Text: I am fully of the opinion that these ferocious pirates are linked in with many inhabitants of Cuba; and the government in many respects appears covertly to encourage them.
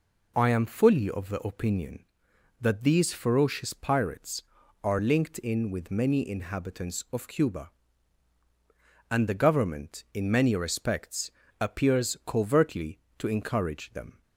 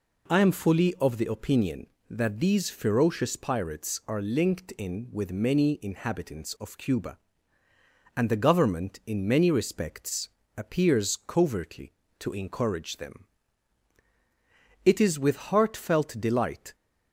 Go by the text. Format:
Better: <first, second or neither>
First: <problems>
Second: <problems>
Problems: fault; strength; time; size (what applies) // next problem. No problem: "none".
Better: first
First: pauses between "respects" and "appears"; slight; at 11.2 s; 0.30 s long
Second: pauses between "respects" and "appears"; slight; at 10.2 s; 0.26 s long // goes on to say "It is with heartfelt delight"; strong; from 14.8 s on; 1.9 s long